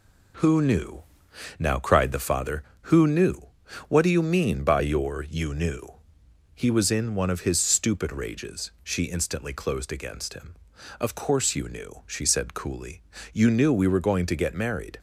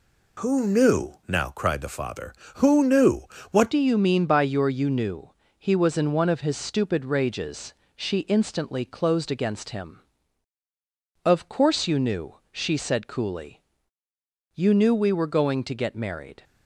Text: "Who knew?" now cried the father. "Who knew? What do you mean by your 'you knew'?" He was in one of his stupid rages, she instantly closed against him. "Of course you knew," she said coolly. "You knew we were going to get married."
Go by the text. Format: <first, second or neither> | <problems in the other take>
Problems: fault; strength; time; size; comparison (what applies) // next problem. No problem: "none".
first | changes voice at "do"; from 3.7 s on; 12.7 s long